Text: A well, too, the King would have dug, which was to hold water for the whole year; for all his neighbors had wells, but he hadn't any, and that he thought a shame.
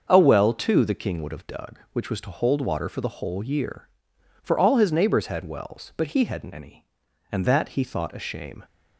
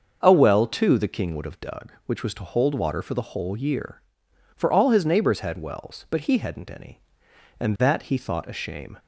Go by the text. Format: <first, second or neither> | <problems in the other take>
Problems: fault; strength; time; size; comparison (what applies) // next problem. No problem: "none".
second | starts louder than the rest; until 1.1 s; 6.5 dB; also in the second // changes voice from "any" to "and"; from 6.5 to 7.4 s; 0.9 s long